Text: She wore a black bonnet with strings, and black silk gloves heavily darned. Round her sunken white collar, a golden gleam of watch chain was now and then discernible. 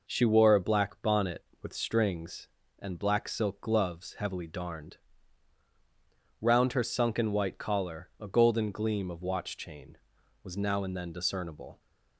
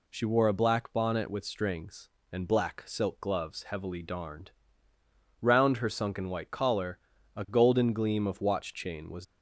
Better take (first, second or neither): first